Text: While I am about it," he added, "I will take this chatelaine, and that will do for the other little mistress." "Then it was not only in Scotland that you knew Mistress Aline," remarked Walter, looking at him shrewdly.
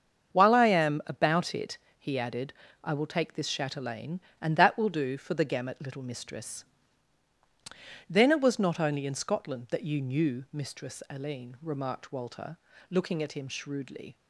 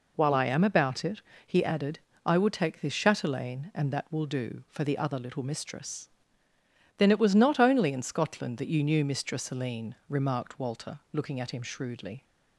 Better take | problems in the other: second | starts louder than the rest; until 1.3 s; 7 dB // says "gamut" for "other"; at 5.4 s

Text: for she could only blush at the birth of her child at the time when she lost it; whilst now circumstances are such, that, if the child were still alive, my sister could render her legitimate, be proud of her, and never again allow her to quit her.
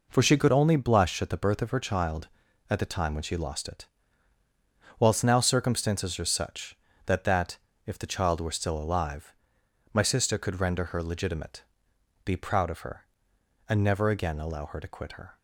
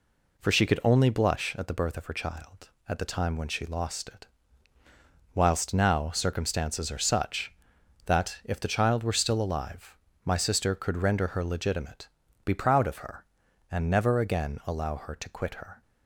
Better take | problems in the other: second | says "that" twice; at 7.2 s

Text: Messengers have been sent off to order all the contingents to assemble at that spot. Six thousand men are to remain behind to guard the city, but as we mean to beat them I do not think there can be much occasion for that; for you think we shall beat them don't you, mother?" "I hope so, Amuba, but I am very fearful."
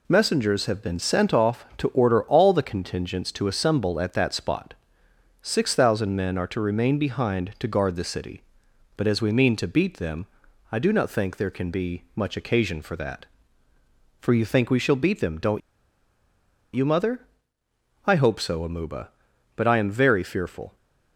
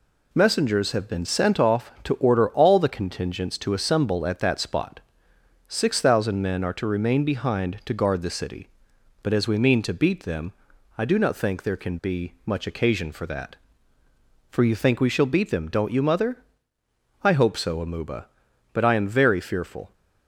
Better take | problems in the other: second | pauses between "them" and "I"; at 10.2 s; 0.44 s long; also in the second // pauses between "don't" and "you"; at 15.6 s; 1.1 s long

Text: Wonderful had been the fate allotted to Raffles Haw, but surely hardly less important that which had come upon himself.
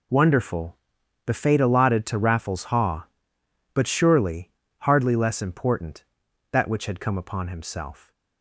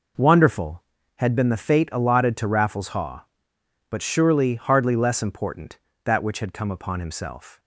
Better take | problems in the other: second | skips "had been"; at 1.0 s // pauses between "surely" and "hardly"; slight; at 4.4 s; 0.30 s long

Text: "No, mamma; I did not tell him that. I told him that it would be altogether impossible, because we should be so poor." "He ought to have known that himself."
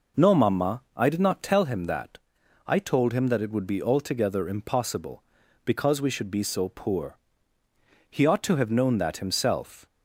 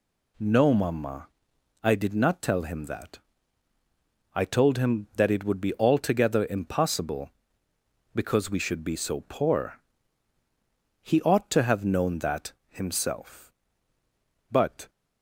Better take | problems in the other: first | pauses between "that" and "himself"; slight; at 12.5 s; 0.16 s long // goes on to say "But"; slight; from 14.5 s on; 0.38 s long

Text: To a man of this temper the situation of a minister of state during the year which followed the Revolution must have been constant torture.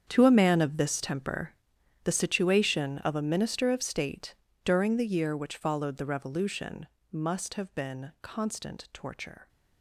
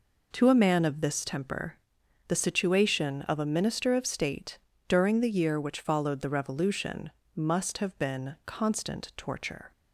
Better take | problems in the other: second | gets quieter; strong; throughout; 16 dB // pauses between "temper" and "the"; noticeable; at 1.5 s; 0.52 s long; noticeable in the second // pauses between "state" and "during"; slight; at 4.3 s; 0.30 s long; slight in the second // pauses between "Revolution" and "must"; slight; at 6.8 s; 0.24 s long; slight in the second

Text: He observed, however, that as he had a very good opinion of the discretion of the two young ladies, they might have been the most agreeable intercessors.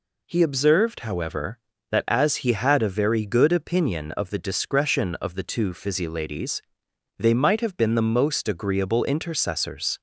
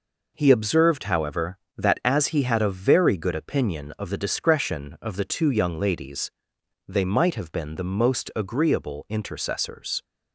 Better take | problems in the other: second | says "physi" for "young"; at 5.7 s

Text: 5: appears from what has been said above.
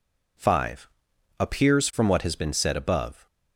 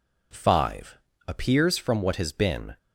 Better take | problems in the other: first | stops before "said above"; at 2.7 s

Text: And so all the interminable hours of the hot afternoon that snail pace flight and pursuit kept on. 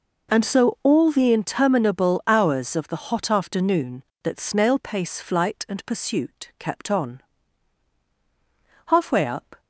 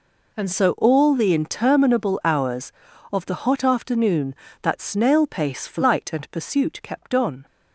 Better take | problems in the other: second | goes on to say "Halfway up"; noticeable; from 8.8 s on; 0.74 s long

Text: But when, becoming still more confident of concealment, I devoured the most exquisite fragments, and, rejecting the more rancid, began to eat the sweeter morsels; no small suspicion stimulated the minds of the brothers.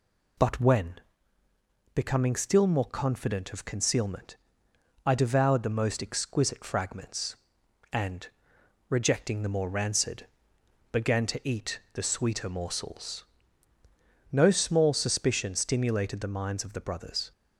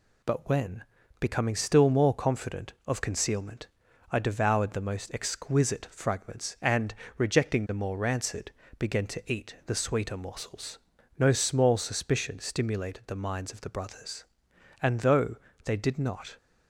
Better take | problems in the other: first | goes on to say "And though they did not"; from 14.8 s on; 1.5 s long

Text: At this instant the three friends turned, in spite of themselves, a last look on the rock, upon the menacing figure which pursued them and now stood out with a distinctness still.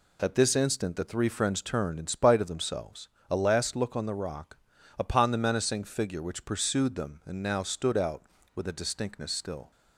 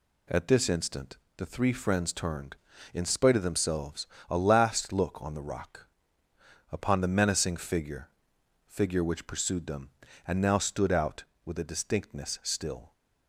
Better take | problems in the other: first | pauses between "instant" and "the"; slight; at 1.1 s; 0.20 s long // says "figure" twice; at 8.6 s

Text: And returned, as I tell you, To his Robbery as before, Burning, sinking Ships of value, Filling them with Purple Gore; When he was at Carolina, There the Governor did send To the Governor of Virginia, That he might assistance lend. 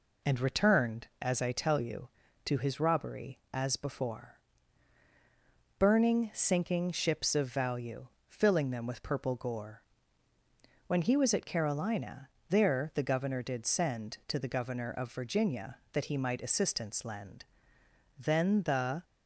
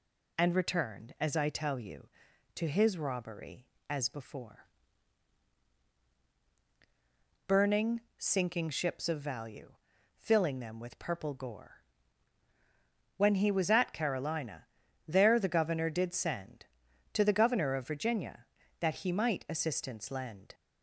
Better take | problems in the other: second | goes on to say "Then the"; noticeable; from 18.1 s on; 0.86 s long

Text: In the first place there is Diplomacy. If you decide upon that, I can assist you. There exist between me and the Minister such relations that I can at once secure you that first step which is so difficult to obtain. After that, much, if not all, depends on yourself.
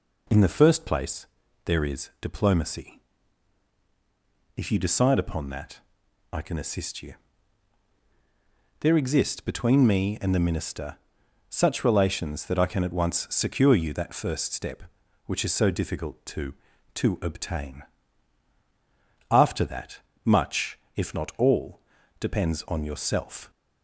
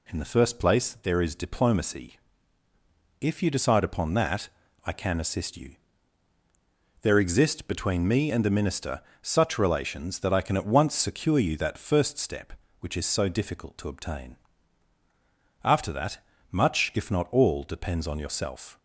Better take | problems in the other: second | pauses between "place" and "there"; at 1.2 s; 0.38 s long // pauses between "Minister" and "such"; noticeable; at 10.9 s; 0.50 s long; slight in the second // says "to" twice; at 16.9 s

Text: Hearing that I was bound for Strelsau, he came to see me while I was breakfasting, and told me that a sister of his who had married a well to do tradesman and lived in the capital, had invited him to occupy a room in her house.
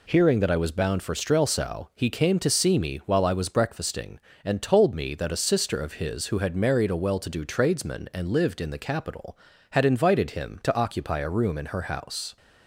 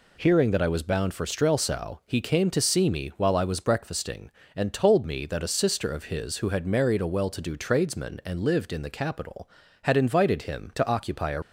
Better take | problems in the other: first | stops before "room in her house"; at 11.4 s

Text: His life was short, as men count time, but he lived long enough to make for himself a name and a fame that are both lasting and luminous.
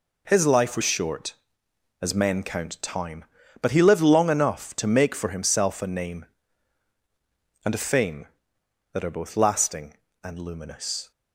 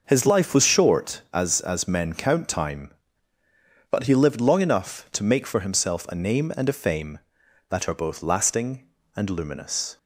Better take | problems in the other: first | starts louder than the rest; noticeable; until 1.0 s; 6 dB // says "as" twice; at 1.6 s

